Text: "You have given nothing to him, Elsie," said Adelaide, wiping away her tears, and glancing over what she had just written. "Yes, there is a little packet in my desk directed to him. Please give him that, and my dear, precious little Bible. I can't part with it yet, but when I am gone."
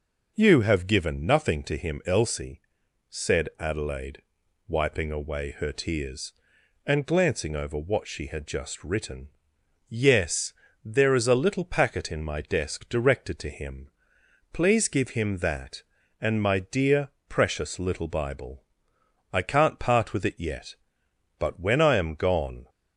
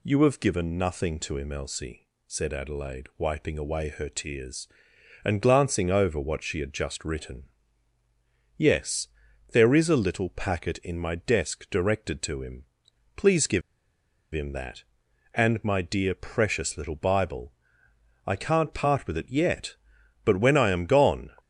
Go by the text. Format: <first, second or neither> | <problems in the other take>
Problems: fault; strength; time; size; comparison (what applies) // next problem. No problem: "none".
first | pauses between "give" and "him"; noticeable; at 13.6 s; 0.72 s long